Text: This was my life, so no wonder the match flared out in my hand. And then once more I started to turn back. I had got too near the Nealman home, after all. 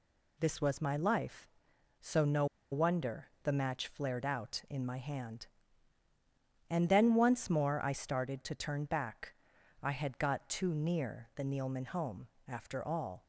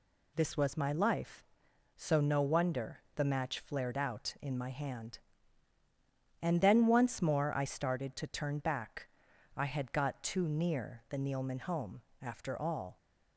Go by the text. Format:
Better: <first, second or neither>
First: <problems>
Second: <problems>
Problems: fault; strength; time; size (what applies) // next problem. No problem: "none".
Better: second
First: pauses between "no" and "wonder"; slight; at 2.4 s; 0.26 s long // pauses between "wonder" and "the"; slight; at 3.2 s; 0.16 s long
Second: pauses between "wonder" and "the"; slight; at 3.0 s; 0.16 s long